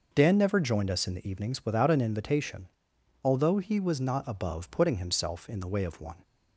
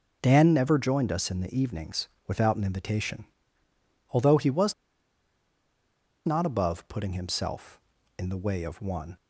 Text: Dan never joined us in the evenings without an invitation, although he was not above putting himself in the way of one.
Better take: first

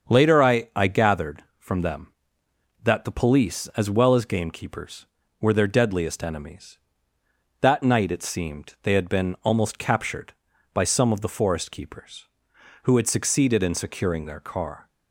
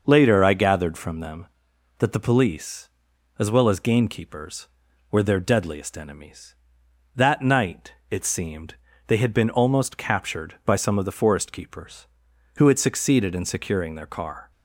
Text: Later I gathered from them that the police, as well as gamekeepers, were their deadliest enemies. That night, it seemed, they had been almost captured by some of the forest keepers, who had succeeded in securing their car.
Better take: second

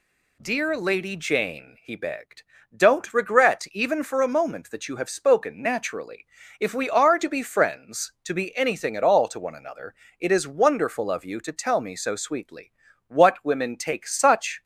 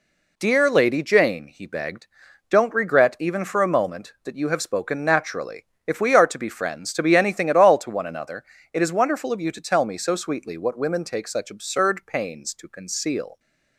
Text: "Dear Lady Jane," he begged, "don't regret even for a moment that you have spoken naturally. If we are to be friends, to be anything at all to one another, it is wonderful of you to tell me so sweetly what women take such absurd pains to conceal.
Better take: second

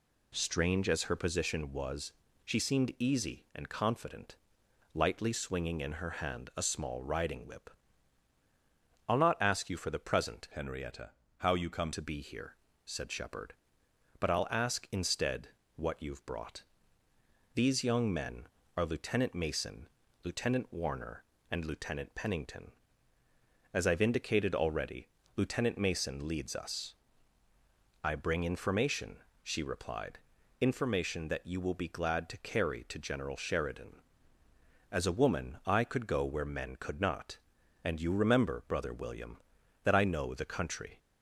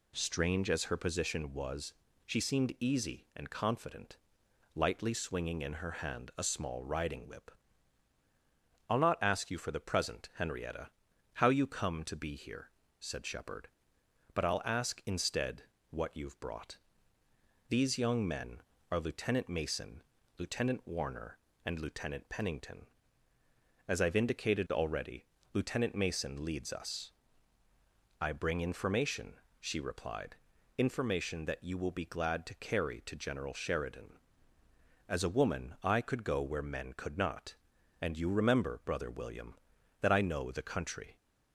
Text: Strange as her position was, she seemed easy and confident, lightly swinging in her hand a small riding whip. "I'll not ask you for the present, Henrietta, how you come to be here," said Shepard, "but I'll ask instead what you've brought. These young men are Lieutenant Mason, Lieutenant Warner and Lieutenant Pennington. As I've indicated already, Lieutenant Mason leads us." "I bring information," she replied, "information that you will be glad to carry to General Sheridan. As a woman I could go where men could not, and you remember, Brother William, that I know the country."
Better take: second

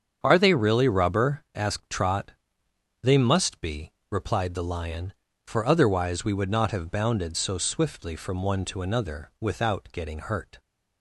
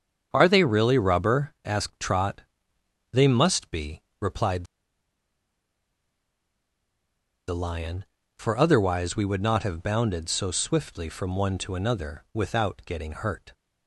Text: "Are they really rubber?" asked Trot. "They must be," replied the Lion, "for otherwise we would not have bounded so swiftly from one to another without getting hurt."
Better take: first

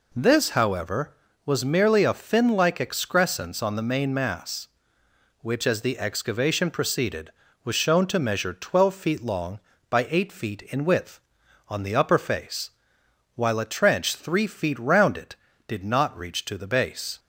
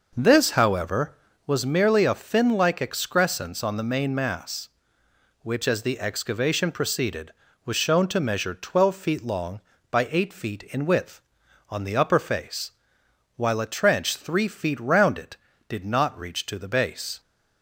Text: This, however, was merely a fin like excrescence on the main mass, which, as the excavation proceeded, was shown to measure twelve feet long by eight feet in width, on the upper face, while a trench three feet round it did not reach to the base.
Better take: first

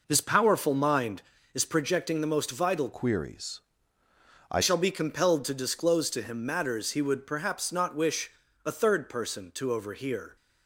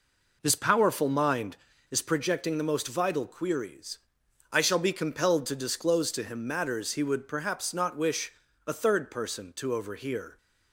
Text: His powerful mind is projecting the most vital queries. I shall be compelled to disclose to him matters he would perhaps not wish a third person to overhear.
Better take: second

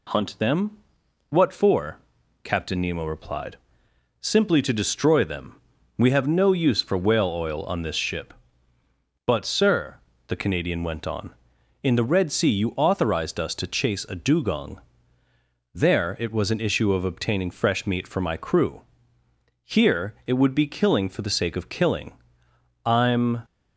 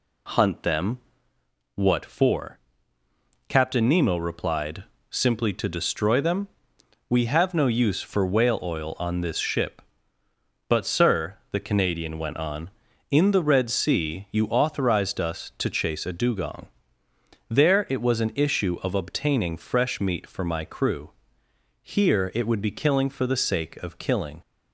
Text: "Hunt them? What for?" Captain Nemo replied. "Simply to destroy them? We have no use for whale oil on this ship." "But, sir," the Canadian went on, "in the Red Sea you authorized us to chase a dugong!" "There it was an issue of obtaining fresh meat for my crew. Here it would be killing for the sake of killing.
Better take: second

